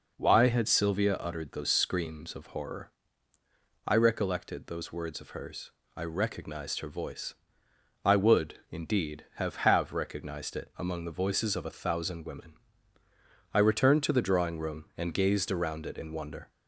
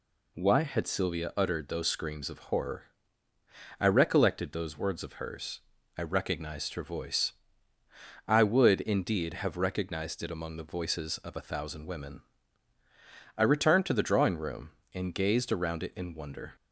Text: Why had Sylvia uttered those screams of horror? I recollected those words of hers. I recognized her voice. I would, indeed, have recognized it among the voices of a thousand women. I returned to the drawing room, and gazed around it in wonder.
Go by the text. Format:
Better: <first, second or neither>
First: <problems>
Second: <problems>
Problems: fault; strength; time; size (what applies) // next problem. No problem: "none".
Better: second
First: says "have" twice; at 9.5 s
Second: none